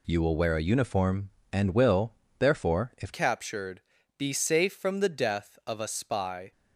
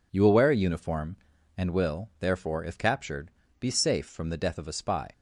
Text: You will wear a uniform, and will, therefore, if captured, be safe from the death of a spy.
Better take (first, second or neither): second